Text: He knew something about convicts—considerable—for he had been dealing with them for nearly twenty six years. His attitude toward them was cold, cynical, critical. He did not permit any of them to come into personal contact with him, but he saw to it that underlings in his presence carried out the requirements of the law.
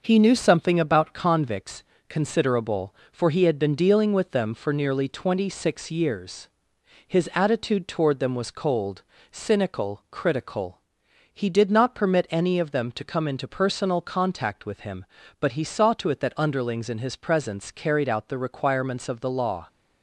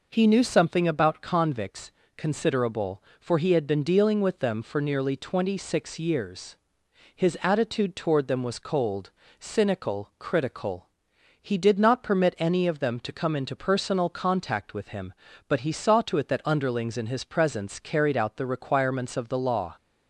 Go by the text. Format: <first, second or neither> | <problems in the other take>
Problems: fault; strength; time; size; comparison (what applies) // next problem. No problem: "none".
second | gets quieter; noticeable; throughout; 4 dB